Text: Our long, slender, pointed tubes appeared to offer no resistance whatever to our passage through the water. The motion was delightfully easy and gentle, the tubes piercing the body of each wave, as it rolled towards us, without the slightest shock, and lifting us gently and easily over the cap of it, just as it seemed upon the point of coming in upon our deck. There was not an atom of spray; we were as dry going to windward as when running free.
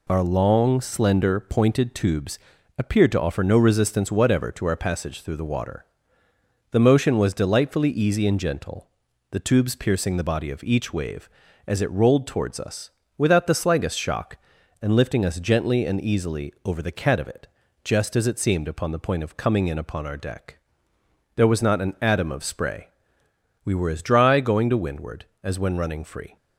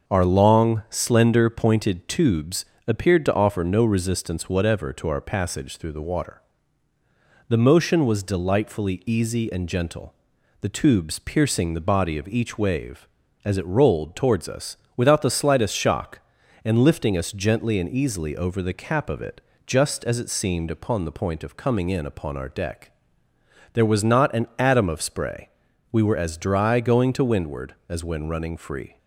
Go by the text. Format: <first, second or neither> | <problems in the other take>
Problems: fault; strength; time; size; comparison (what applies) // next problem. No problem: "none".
second | pauses between "tubes" and "appeared"; at 2.3 s; 0.40 s long; slight in the second // says "cat" for "cap"; at 16.9 s